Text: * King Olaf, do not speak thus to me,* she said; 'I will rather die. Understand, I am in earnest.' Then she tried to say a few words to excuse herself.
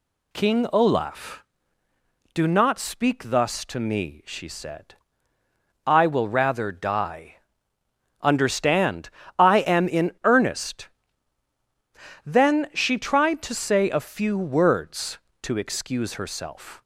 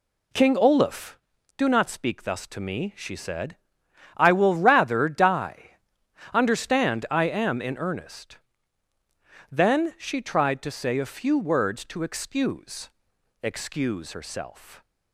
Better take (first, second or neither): first